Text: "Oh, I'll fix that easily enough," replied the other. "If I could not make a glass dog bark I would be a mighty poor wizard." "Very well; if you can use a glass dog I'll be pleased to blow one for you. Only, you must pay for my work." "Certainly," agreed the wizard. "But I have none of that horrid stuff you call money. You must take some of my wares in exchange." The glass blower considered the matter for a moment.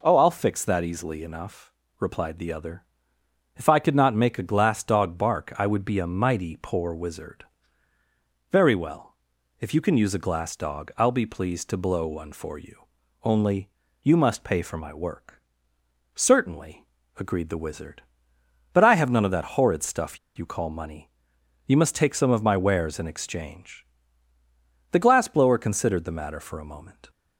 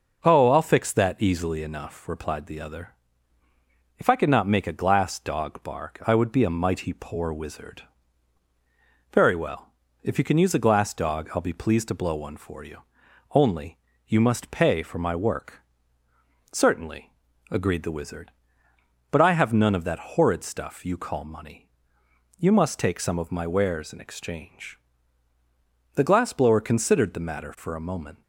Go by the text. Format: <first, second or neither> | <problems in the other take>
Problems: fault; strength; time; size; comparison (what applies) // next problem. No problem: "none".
second | pauses between "stuff" and "you"; slight; at 20.1 s; 0.19 s long